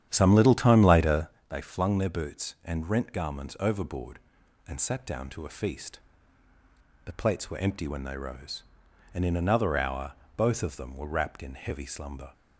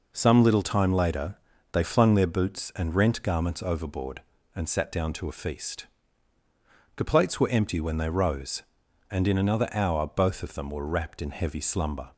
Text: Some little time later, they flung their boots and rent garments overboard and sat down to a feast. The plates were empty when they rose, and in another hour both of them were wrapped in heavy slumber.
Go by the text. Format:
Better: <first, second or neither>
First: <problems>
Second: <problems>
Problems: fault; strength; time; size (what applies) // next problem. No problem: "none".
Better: second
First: starts louder than the rest; strong; until 1.5 s; 10 dB // pauses between "hour" and "both"; slight; at 10.1 s; 0.24 s long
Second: none